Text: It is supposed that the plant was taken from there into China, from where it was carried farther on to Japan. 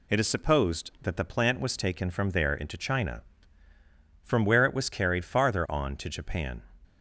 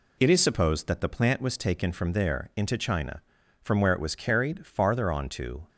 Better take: first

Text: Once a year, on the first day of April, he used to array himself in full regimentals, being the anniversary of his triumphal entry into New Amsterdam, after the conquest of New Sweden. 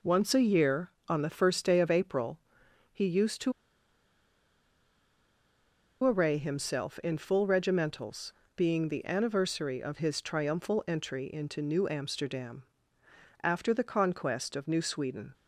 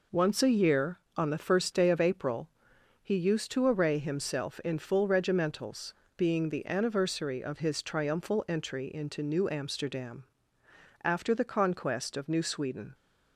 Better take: second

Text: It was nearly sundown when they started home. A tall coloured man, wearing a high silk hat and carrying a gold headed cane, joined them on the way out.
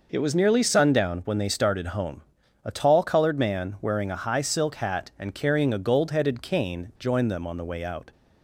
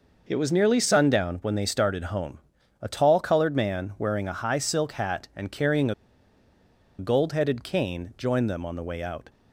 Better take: first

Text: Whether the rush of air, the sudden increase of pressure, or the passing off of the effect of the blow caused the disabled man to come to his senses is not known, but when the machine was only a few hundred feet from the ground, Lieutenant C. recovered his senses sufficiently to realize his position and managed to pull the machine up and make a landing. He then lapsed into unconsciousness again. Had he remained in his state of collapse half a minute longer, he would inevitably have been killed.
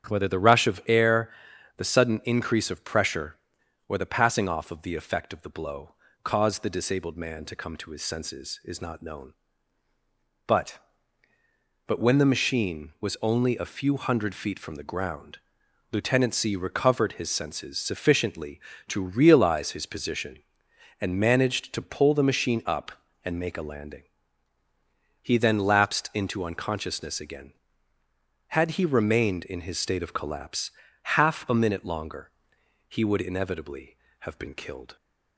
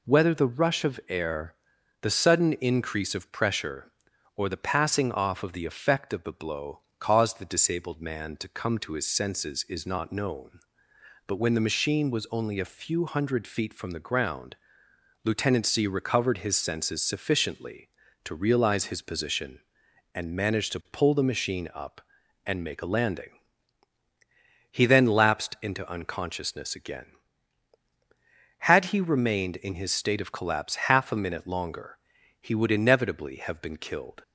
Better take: second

